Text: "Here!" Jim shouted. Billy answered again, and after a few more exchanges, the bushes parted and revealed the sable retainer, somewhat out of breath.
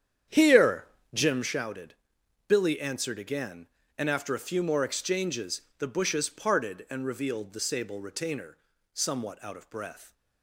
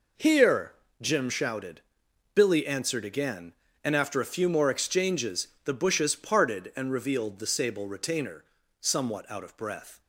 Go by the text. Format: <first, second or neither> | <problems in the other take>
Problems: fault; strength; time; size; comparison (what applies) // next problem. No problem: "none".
second | starts louder than the rest; strong; until 1.6 s; 9 dB